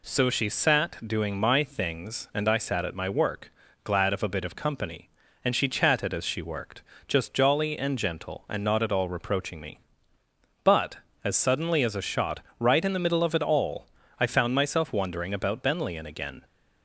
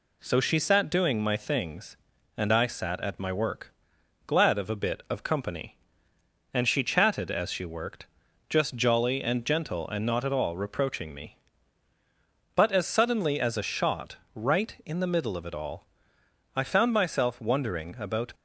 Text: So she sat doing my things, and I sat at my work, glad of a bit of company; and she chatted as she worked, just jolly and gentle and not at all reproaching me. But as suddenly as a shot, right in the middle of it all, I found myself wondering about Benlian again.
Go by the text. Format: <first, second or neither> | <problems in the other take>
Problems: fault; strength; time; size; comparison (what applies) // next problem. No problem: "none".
first | stops before "Benlian again"; at 18.3 s